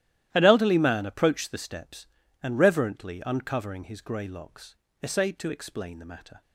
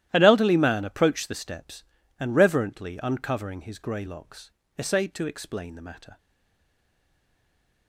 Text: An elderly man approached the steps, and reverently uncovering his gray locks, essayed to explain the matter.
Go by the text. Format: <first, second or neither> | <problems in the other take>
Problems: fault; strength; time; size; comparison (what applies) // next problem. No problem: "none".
first | starts louder than the rest; strong; until 1.1 s; 13.5 dB; strong in the first // stays silent after the last word; noticeable; from 6.1 s on; 1.7 s long